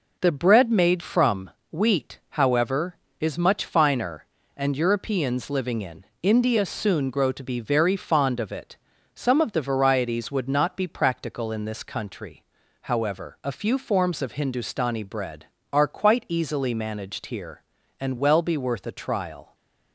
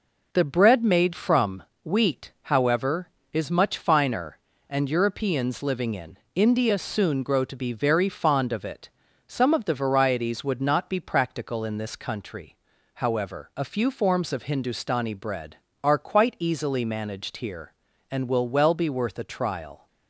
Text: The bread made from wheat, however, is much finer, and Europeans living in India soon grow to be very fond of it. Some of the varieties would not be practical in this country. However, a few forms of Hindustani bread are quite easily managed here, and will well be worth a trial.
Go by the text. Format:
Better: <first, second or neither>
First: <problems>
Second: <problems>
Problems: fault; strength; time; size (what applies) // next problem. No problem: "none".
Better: second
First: pauses between "from" and "wheat"; slight; at 1.5 s; 0.18 s long // pauses between "in" and "India"; slight; at 6.0 s; 0.18 s long // skips "will"; at 18.1 s // stays silent after the last word; slight; from 19.4 s on; 0.5 s long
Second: pauses between "from" and "wheat"; slight; at 1.6 s; 0.18 s long // pauses between "in" and "India"; slight; at 6.1 s; 0.18 s long